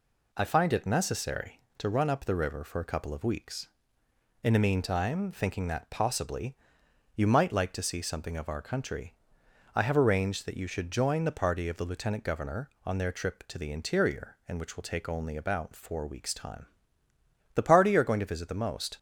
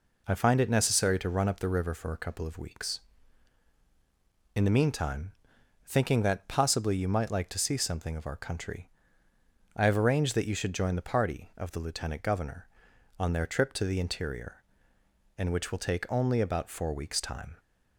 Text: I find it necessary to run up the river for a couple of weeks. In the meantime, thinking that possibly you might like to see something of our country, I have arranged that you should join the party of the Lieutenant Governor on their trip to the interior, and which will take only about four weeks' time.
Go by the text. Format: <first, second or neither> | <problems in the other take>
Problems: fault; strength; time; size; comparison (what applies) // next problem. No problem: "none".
second | pauses between "possibly" and "you"; noticeable; at 6.5 s; 0.60 s long // goes on to say "The party are going to visit the most"; from 17.5 s on; 1.4 s long